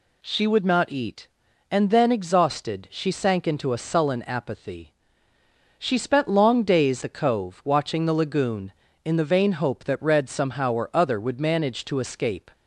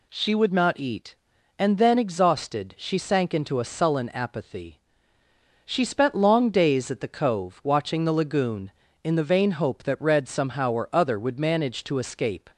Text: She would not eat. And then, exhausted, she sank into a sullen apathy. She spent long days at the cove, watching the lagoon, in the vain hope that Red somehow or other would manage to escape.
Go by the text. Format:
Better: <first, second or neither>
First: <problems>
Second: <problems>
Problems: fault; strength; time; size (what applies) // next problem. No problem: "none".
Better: second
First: skips "at"; at 7.0 s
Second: none